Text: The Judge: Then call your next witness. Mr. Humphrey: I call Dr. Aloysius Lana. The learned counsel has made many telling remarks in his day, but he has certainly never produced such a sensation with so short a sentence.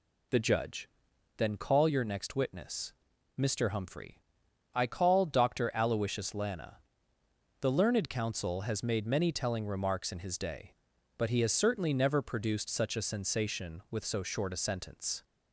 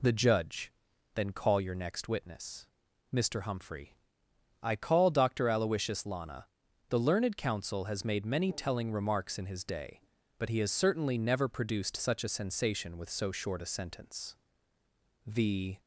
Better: first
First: none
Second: goes on to say "The"; from 15.2 s on; 0.54 s long

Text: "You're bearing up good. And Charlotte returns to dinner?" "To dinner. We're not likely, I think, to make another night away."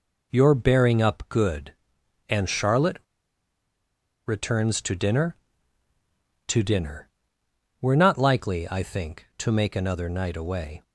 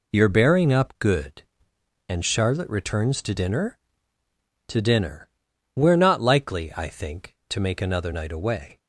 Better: second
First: pauses between "Charlotte" and "returns"; strong; at 2.9 s; 1.2 s long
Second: none

